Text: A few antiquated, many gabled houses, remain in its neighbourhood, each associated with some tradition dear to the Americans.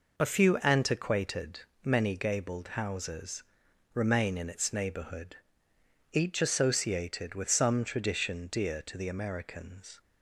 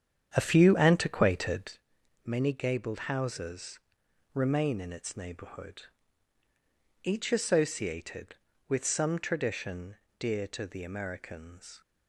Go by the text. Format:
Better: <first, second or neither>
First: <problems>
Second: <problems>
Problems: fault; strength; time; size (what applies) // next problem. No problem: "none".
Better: first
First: none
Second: starts louder than the rest; strong; until 1.8 s; 8.5 dB // pauses between "tradition" and "dear"; slight; at 9.9 s; 0.22 s long